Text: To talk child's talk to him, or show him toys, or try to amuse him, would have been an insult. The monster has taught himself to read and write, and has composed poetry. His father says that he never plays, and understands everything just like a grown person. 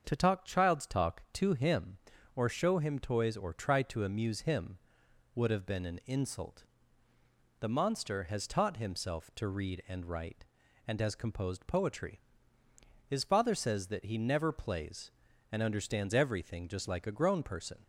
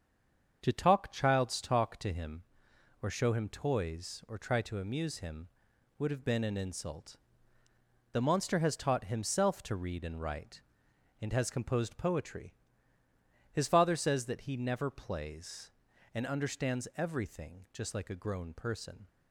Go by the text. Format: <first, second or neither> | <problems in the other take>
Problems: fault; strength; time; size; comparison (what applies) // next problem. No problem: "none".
first | stays silent before the first word; slight; until 0.6 s; 0.6 s long // starts louder than the rest; until 1.6 s; 7 dB; also in the first